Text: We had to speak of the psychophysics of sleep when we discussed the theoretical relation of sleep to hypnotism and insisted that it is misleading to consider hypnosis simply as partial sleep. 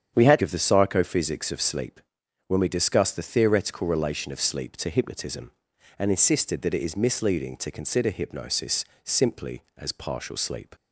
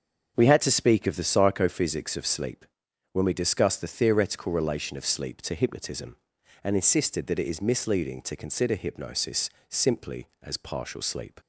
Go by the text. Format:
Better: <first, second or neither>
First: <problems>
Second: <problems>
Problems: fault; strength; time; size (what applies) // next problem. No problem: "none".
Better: second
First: starts louder than the rest; strong; until 1.1 s; 8.5 dB // skips "to speak"; at 0.4 s // pauses between "sleep" and "when"; noticeable; at 2.0 s; 0.46 s long // pauses between "hypnosis" and "simply"; slight; at 8.8 s; 0.20 s long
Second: starts louder than the rest; until 1.3 s; 7 dB // pauses between "sleep" and "when"; noticeable; at 2.6 s; 0.46 s long // pauses between "hypnosis" and "simply"; slight; at 9.4 s; 0.20 s long